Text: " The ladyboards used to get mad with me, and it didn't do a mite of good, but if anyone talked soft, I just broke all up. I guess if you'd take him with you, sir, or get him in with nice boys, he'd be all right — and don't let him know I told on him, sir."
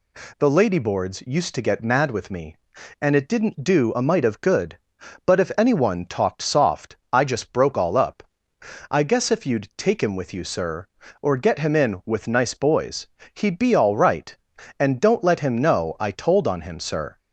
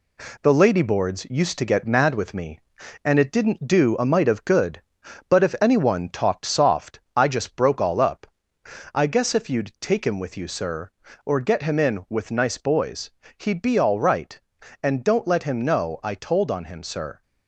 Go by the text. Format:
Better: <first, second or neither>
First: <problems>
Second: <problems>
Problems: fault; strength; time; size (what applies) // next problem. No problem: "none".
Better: first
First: none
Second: gets quieter; slight; throughout; 3 dB